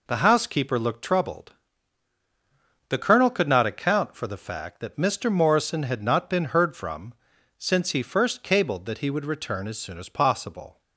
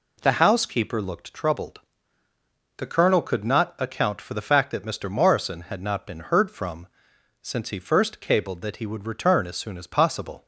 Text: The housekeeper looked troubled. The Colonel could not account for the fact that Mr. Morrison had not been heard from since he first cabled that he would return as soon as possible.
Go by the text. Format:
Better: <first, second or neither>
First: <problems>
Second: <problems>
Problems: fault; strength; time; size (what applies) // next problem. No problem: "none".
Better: neither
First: pauses between "from" and "since"; at 7.1 s; 0.44 s long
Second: pauses between "from" and "since"; noticeable; at 6.8 s; 0.54 s long